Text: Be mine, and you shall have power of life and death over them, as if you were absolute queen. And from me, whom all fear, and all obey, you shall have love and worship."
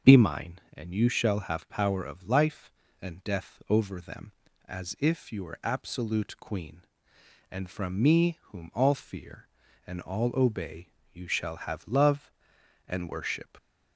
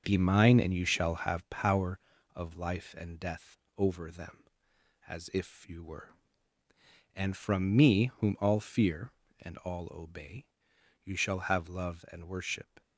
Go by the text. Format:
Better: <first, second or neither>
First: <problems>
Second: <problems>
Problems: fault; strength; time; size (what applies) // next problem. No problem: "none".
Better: first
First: starts louder than the rest; until 1.1 s; 6.5 dB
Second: starts louder than the rest; noticeable; until 1.0 s; 6 dB // pauses between "death" and "over"; slight; at 3.5 s; 0.18 s long // skips "absolute queen"; at 6.6 s